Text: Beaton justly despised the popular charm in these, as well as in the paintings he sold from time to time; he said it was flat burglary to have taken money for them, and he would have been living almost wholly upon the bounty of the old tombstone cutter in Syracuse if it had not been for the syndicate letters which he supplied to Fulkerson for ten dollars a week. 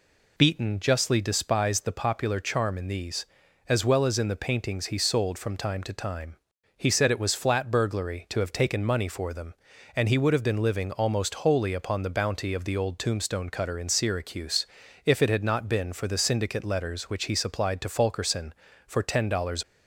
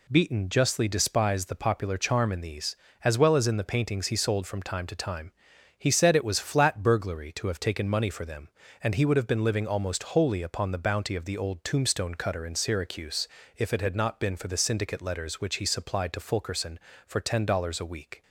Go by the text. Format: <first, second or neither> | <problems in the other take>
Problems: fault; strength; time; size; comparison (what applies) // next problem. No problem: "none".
second | pauses between "Syracuse" and "if"; at 14.6 s; 0.40 s long; slight in the second // stops before "a week"; at 19.6 s